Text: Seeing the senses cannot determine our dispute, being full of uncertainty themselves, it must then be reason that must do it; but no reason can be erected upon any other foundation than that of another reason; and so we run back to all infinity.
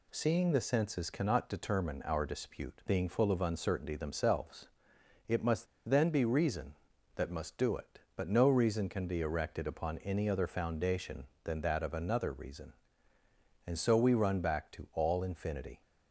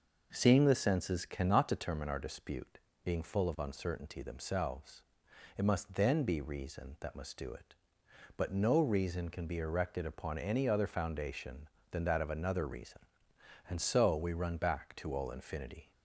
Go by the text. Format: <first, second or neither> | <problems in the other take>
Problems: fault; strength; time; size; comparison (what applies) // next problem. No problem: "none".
second | pauses between "must" and "then"; slight; at 5.6 s; 0.22 s long